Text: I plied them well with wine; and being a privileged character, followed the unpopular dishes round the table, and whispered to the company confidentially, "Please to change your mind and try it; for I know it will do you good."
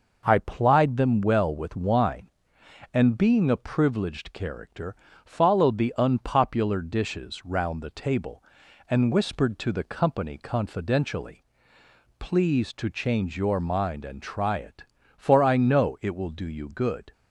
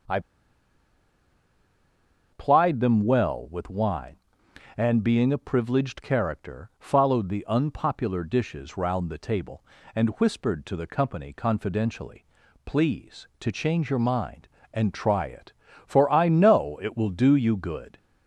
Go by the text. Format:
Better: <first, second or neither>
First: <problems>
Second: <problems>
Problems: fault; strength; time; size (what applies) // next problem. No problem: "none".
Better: first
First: none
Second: starts louder than the rest; until 3.2 s; 6.5 dB // pauses between "I" and "plied"; strong; at 0.2 s; 2.1 s long